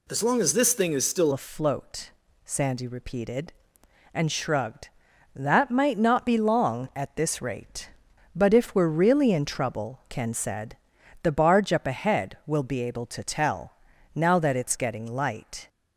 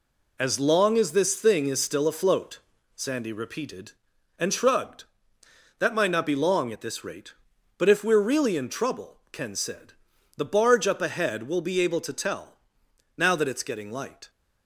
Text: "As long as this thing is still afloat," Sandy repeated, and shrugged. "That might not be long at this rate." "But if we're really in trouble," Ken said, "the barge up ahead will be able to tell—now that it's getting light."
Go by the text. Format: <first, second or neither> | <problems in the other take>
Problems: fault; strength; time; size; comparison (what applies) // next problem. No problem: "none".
second | changes voice at "afloat"; from 1.3 s on; 14.3 s long